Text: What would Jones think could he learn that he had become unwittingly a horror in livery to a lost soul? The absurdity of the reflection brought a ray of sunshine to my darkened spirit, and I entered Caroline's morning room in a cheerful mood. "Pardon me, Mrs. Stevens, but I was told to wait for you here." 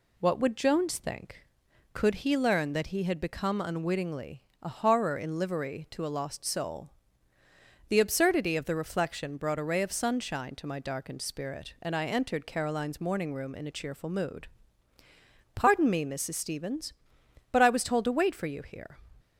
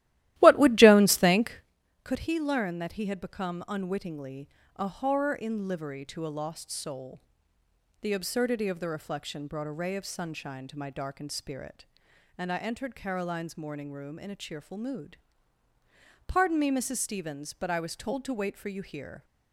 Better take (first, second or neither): first